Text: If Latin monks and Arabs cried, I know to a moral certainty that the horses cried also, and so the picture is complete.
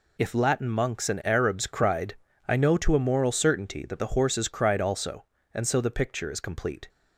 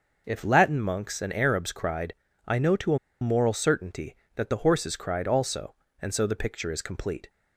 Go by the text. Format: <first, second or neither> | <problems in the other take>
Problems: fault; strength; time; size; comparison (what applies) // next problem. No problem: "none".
first | pauses between "a" and "moral"; slight; at 2.9 s; 0.22 s long